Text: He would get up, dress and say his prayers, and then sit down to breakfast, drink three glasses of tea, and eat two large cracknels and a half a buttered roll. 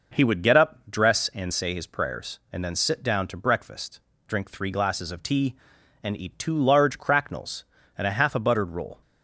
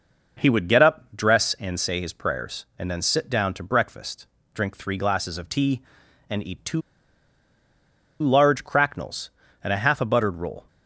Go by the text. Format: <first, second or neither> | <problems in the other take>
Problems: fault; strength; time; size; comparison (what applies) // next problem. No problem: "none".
first | pauses between "two" and "large"; strong; at 6.8 s; 1.4 s long